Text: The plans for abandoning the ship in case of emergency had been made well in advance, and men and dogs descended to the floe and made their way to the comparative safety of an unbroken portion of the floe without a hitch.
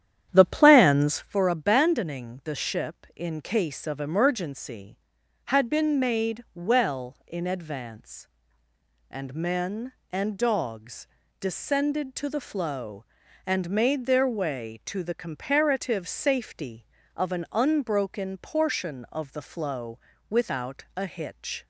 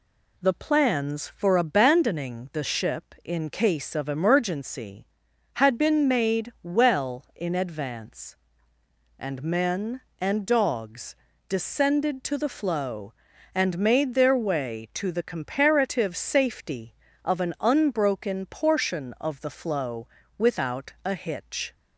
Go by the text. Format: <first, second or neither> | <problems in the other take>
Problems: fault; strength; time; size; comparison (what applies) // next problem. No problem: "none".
second | starts louder than the rest; strong; until 1.3 s; 10 dB // pauses between "dogs" and "descended"; slight; at 11.0 s; 0.34 s long; slight in the second // pauses between "floe" and "without"; slight; at 19.9 s; 0.30 s long; slight in the second